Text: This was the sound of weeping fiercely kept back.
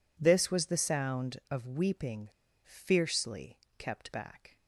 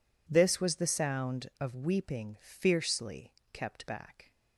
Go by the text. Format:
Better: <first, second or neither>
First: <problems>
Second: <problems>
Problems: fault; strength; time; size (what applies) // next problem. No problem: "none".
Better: second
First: pauses between "weeping" and "fiercely"; at 2.2 s; 0.38 s long // pauses between "fiercely" and "kept"; slight; at 3.5 s; 0.20 s long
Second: pauses between "fiercely" and "kept"; slight; at 3.3 s; 0.20 s long